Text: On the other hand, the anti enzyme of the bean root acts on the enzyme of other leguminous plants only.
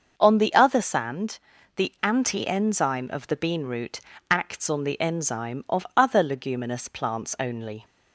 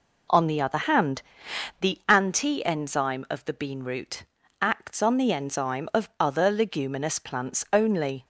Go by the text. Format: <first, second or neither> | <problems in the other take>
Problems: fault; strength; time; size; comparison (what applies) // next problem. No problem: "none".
second | starts louder than the rest; until 1.1 s; 6.5 dB // says "sand" for "hand"; at 0.7 s // pauses between "root" and "acts"; slight; at 4.0 s; 0.28 s long; slight in the second